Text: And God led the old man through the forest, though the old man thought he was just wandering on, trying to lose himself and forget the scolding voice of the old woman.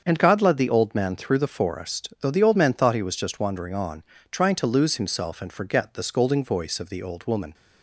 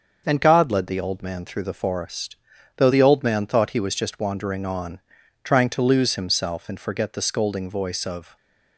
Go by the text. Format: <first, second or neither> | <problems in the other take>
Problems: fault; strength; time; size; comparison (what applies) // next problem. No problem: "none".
first | starts louder than the rest; until 1.2 s; 6.5 dB; also in the first // stops before "the old woman"; at 8.3 s